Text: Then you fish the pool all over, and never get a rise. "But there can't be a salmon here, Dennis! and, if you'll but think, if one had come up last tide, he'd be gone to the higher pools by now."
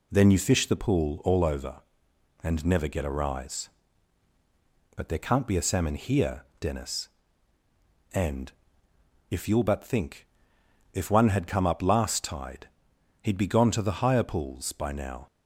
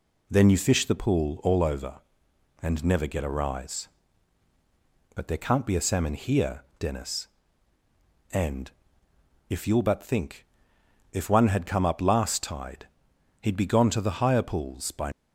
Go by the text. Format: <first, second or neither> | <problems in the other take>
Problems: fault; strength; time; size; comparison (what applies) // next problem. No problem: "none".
first | stops before "now"; at 15.1 s